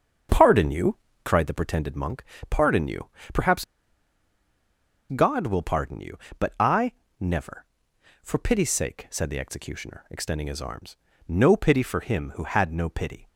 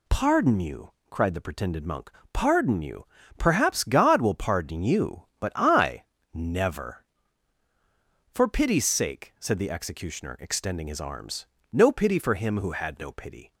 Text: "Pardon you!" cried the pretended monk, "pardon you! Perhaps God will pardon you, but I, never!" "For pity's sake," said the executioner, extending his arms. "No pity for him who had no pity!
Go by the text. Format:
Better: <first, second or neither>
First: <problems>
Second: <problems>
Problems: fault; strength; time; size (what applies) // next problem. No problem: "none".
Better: second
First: starts louder than the rest; until 1.5 s; 7 dB // pauses between "Perhaps" and "God"; strong; at 3.6 s; 1.4 s long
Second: none